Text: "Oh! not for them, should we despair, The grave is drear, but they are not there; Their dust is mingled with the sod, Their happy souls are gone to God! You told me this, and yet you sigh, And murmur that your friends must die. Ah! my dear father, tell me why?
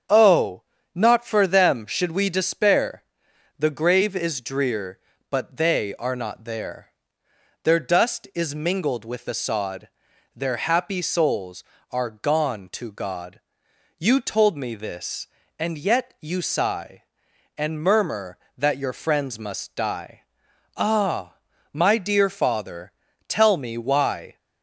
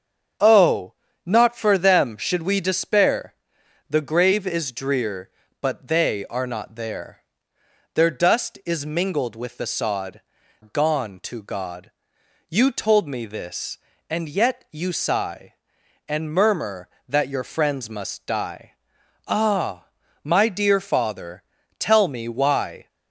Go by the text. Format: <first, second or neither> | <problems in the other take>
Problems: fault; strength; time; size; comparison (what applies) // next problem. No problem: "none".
first | starts louder than the rest; strong; until 1.7 s; 7.5 dB; strong in the first // skips "Their happy souls are"; at 10.4 s